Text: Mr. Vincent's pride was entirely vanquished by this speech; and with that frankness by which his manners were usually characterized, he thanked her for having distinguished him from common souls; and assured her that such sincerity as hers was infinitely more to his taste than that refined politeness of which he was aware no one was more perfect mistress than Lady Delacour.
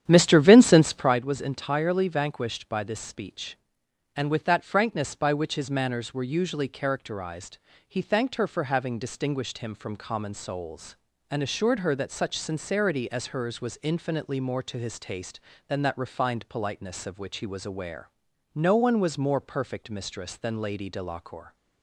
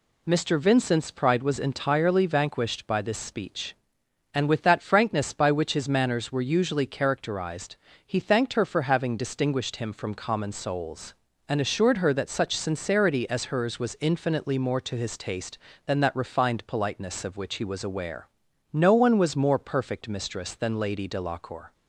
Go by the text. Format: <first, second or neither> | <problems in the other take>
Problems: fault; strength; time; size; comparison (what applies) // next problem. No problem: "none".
second | starts louder than the rest; strong; until 1.2 s; 10 dB // pauses between "aware" and "no"; at 18.1 s; 0.42 s long; also in the second